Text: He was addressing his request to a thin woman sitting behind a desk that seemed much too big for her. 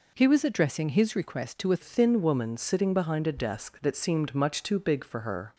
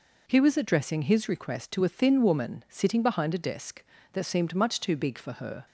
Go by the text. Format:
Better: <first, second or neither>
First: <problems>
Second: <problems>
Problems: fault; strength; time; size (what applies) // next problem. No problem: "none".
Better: second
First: changes voice at "thin"; from 1.8 s on; 3.7 s long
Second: none